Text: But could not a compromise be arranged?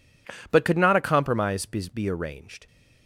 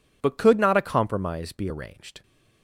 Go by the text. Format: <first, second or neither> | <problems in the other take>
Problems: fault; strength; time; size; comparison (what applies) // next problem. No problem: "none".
second | says "be" twice; at 1.9 s